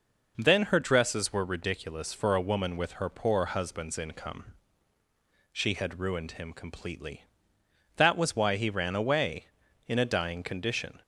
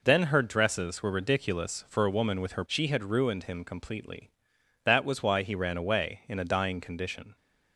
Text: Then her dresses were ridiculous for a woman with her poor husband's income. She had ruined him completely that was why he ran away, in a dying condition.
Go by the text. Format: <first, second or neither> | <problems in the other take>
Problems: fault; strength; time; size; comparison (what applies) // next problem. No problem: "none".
first | skips "poor husband's income"; at 2.6 s